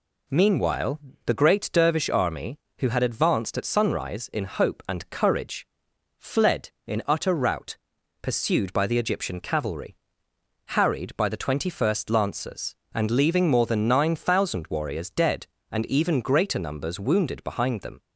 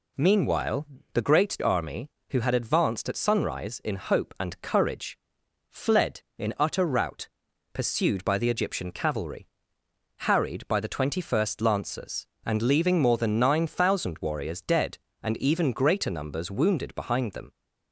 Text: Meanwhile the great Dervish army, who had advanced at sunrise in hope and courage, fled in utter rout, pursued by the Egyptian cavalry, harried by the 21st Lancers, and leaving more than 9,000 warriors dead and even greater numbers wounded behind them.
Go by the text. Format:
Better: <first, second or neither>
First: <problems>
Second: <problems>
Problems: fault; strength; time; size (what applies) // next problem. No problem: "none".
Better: first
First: pauses between "Meanwhile" and "the"; slight; at 0.9 s; 0.26 s long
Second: pauses between "Meanwhile" and "the"; slight; at 0.8 s; 0.28 s long // skips "Dervish"; at 1.5 s